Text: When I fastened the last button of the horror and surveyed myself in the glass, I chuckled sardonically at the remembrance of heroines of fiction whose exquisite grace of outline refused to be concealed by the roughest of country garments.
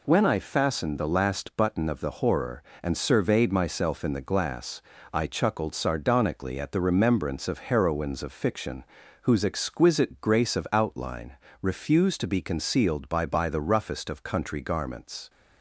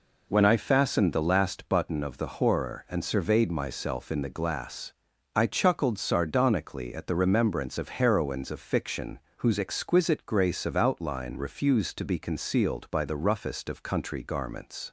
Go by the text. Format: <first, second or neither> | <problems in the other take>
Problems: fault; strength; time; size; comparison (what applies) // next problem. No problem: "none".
second | pauses between "fiction" and "whose"; at 8.8 s; 0.38 s long; slight in the second // pauses between "outline" and "refused"; slight; at 11.3 s; 0.26 s long // says "by" twice; at 13.2 s